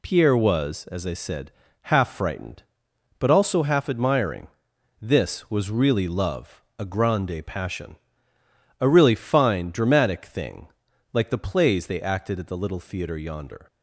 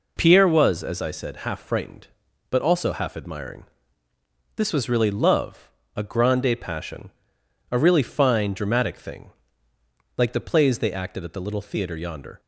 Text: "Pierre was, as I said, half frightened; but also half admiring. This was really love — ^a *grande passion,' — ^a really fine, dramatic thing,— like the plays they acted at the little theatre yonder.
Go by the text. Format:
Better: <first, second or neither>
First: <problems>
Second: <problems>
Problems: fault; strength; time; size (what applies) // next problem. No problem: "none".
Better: neither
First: none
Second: none